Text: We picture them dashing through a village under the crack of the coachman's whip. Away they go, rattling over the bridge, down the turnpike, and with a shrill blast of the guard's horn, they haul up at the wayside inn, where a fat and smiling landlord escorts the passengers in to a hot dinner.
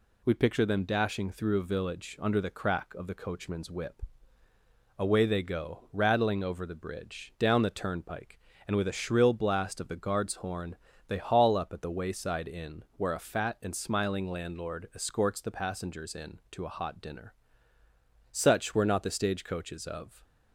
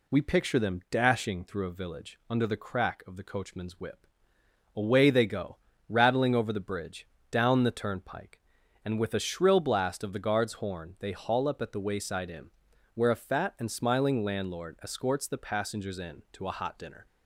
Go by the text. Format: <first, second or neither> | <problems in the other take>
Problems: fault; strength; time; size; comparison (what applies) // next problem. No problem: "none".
second | goes on to say "Such were not the stagecoaches of"; strong; from 18.3 s on; 1.9 s long